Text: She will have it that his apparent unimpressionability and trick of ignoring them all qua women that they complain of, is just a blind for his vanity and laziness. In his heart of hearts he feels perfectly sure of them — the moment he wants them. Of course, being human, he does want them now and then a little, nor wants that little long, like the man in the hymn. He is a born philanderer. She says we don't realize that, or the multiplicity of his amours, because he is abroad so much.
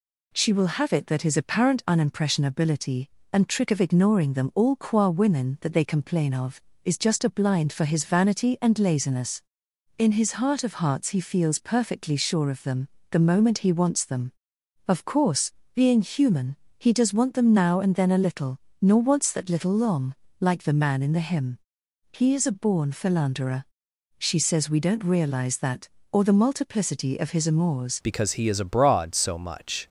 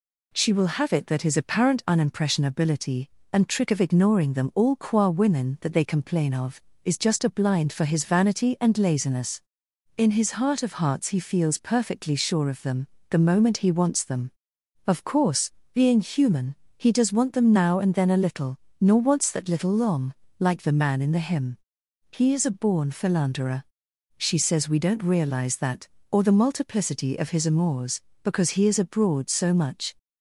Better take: second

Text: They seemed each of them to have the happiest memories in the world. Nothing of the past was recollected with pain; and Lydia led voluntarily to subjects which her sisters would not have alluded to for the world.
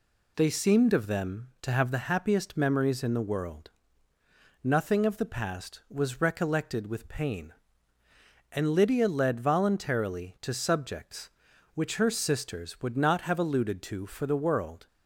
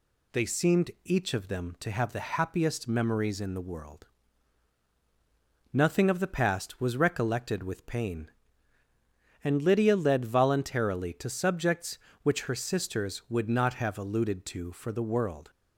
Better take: second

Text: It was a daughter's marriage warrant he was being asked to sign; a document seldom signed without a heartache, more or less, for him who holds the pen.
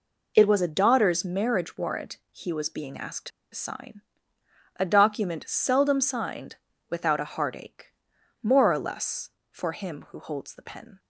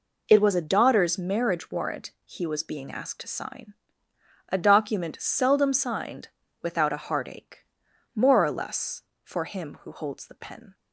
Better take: second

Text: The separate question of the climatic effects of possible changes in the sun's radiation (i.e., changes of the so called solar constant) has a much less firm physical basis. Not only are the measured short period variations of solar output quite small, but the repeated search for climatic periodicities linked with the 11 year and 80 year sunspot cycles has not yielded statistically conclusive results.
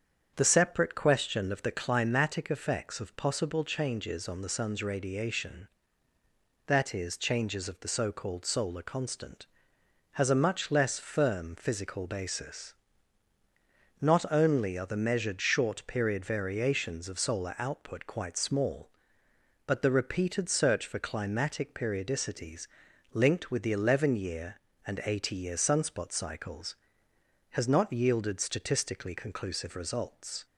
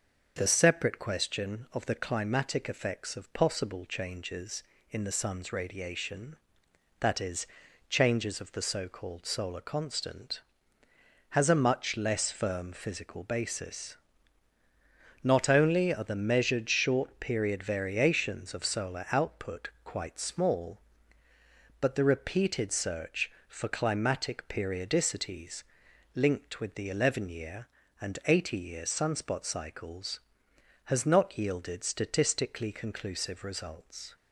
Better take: second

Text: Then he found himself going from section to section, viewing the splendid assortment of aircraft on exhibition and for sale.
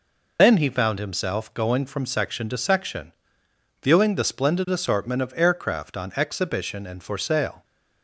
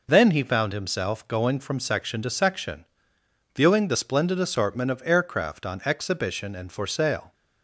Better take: second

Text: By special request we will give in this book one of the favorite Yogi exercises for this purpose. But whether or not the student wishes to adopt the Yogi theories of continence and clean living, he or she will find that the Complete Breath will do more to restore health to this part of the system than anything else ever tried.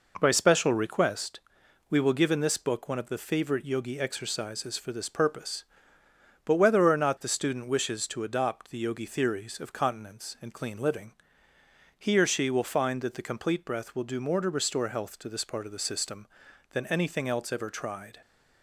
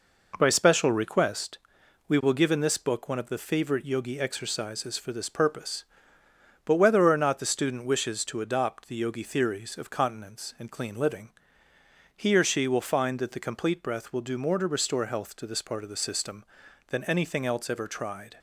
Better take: neither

